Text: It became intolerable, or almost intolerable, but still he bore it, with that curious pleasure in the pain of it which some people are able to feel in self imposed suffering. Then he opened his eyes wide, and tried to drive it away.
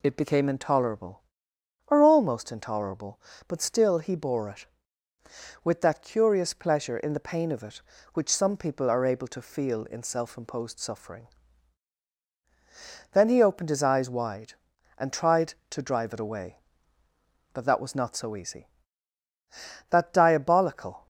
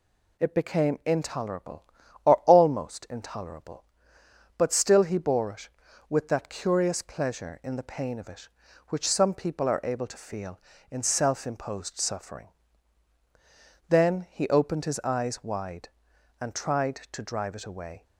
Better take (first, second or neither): second